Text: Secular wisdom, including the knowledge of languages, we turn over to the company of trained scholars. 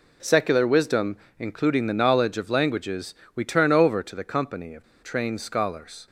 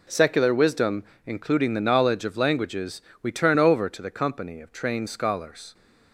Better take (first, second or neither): second